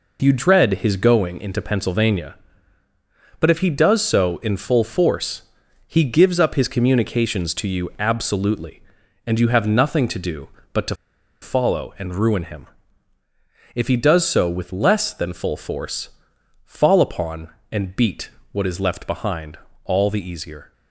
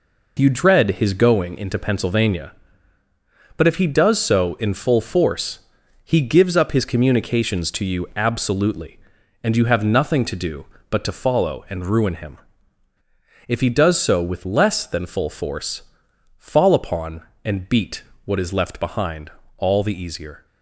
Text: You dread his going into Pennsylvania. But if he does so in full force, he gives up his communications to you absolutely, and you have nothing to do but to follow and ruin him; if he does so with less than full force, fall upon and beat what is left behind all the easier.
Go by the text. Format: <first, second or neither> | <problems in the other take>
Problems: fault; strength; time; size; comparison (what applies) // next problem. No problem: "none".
second | pauses between "to" and "follow"; noticeable; at 10.9 s; 0.47 s long // pauses between "beat" and "what"; slight; at 18.2 s; 0.22 s long; slight in the second // pauses between "behind" and "all"; slight; at 19.5 s; 0.28 s long; slight in the second